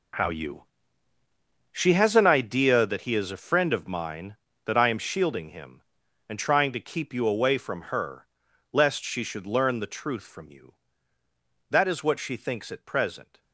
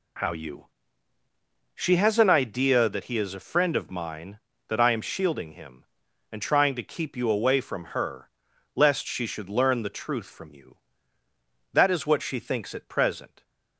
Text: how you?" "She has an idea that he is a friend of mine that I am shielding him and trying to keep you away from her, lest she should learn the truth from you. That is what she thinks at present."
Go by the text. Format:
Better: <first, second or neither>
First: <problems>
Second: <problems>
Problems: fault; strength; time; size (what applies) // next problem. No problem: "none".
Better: second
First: gets quieter; strong; throughout; 12.5 dB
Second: none